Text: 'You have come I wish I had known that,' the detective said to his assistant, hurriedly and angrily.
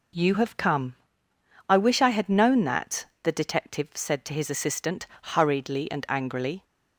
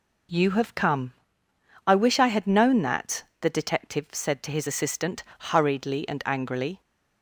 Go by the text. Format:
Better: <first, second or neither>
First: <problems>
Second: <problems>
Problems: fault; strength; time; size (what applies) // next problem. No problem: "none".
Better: neither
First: pauses between "come" and "I"; noticeable; at 0.9 s; 0.76 s long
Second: pauses between "come" and "I"; noticeable; at 1.1 s; 0.76 s long